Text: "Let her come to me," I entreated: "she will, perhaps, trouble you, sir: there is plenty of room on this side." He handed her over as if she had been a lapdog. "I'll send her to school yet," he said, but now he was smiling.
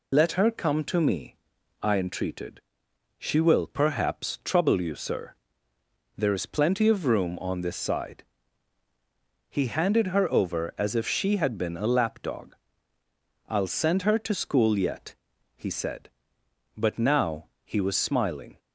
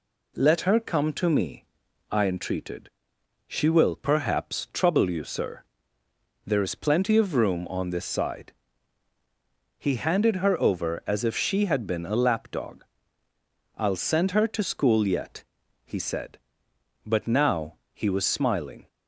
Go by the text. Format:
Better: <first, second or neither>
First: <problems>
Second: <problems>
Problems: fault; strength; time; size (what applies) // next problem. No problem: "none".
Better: second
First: loses the start of "Let"; at 0.1 s; 60 ms // pauses between "now" and "he"; slight; at 17.4 s; 0.18 s long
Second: pauses between "now" and "he"; slight; at 17.7 s; 0.18 s long